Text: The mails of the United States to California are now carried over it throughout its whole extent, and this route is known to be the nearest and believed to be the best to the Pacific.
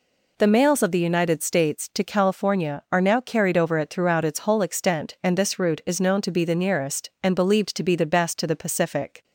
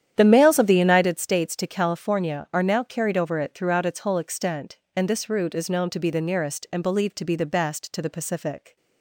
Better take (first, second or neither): first